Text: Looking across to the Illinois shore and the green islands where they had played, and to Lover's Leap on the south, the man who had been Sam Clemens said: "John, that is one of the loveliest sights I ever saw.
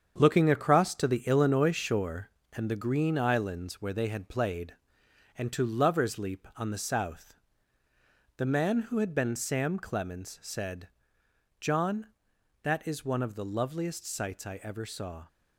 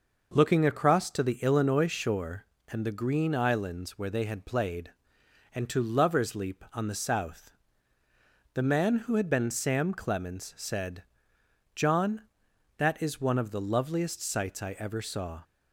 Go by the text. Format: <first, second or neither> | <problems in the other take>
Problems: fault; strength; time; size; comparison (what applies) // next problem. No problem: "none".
second | gets quieter; strong; throughout; 8 dB